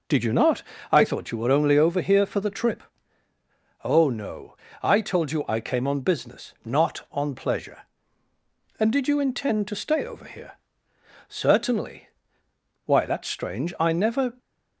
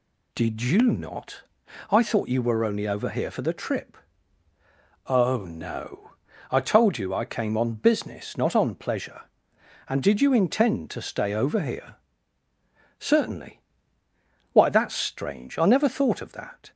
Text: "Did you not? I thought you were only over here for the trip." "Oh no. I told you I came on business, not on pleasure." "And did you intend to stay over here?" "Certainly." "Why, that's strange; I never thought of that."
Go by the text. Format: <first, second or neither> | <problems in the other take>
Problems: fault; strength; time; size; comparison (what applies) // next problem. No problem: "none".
second | stops before "thought of that"; at 14.3 s